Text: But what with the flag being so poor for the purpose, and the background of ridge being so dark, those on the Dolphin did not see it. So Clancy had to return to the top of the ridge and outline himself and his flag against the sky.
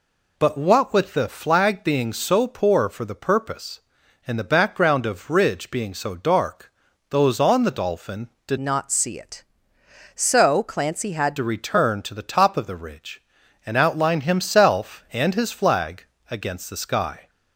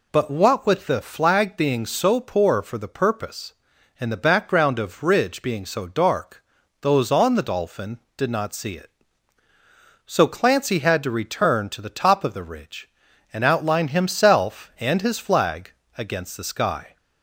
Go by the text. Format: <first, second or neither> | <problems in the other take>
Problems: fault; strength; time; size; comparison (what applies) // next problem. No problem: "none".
second | changes voice from "not" to "had"; from 8.5 to 11.3 s; 2.8 s long // pauses between "flag" and "against"; slight; at 16.0 s; 0.24 s long; slight in the second